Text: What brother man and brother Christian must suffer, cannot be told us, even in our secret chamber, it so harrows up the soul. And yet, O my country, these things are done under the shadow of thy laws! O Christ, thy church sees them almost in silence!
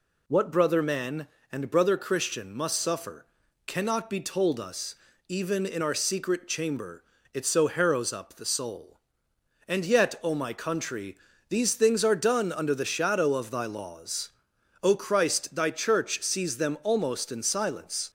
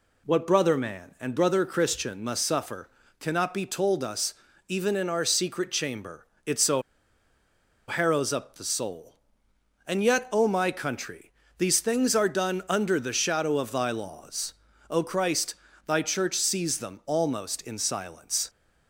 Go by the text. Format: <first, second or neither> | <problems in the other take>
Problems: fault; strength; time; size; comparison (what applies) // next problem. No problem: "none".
first | pauses between "so" and "harrows"; at 6.8 s; 1.0 s long